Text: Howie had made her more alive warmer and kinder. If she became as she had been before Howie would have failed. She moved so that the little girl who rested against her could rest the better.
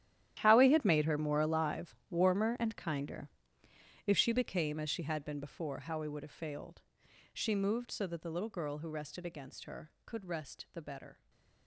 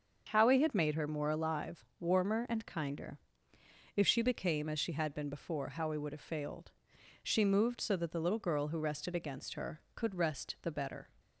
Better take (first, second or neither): second